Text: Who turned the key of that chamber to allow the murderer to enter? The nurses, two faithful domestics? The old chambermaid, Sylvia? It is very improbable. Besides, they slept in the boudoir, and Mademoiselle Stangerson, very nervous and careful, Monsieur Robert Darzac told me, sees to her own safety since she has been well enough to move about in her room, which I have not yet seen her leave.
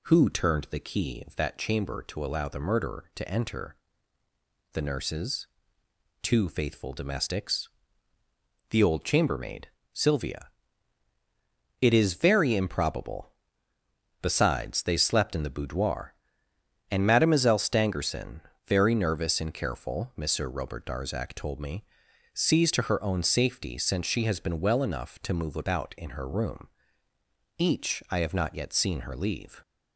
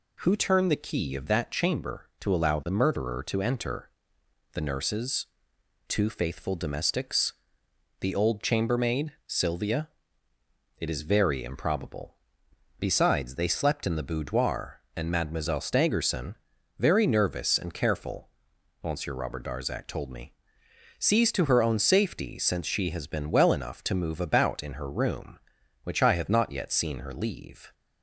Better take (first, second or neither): second